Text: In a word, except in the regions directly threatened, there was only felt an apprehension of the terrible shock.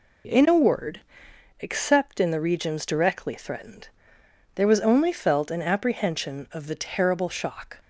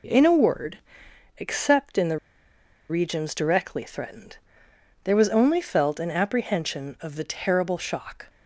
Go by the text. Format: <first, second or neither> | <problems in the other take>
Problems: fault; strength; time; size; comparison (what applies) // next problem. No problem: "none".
first | pauses between "the" and "regions"; noticeable; at 2.1 s; 0.71 s long